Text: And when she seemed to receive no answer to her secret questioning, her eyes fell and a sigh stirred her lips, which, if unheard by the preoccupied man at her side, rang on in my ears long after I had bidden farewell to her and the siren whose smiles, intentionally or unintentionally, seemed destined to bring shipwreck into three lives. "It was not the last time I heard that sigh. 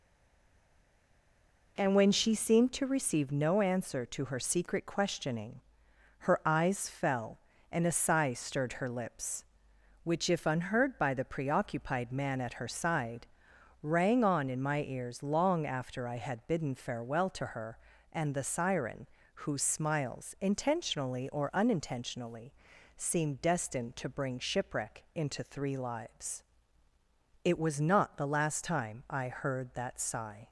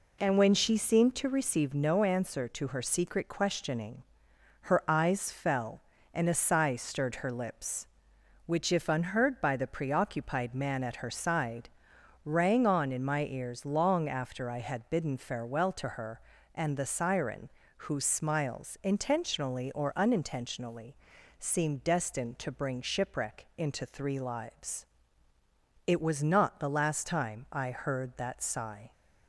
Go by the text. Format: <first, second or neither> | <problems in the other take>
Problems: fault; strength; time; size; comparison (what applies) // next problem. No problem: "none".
second | stays silent before the first word; noticeable; until 1.7 s; 1.7 s long // pauses between "siren" and "whose"; slight; at 19.0 s; 0.36 s long; slight in the second